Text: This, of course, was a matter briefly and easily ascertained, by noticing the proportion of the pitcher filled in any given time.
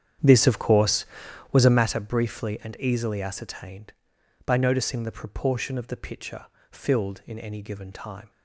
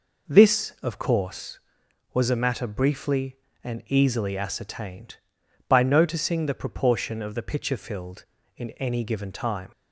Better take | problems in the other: second | starts louder than the rest; strong; until 1.9 s; 9 dB // pauses between "pitcher" and "filled"; slight; at 6.4 s; 0.24 s long

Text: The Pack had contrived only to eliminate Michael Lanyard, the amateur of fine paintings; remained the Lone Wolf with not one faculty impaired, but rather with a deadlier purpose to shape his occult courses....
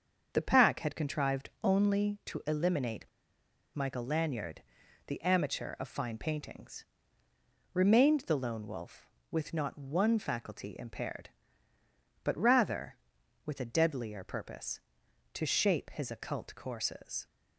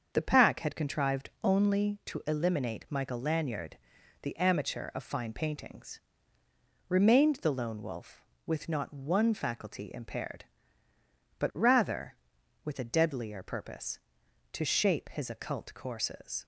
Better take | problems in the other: second | starts louder than the rest; until 1.3 s; 7 dB; also in the second // pauses between "contrived" and "only"; slight; at 1.4 s; 0.16 s long; slight in the second // pauses between "eliminate" and "Michael"; noticeable; at 3.0 s; 0.67 s long

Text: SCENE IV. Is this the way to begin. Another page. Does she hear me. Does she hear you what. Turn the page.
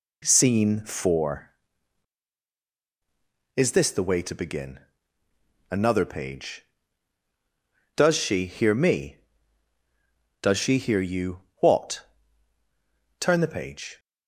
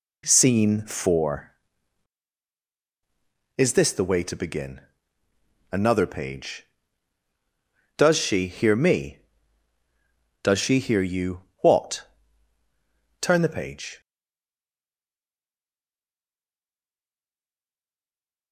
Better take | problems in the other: first | pauses between "you" and "what"; slight; at 11.4 s; 0.16 s long; slight in the first // stays silent after the last word; strong; from 14.0 s on; 4.5 s long

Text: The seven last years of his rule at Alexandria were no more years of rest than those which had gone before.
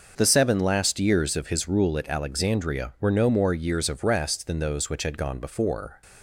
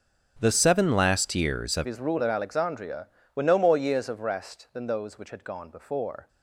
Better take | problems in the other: first | starts louder than the rest; strong; until 1.4 s; 7 dB; noticeable in the first // changes voice at "his"; from 1.8 s on; 4.4 s long

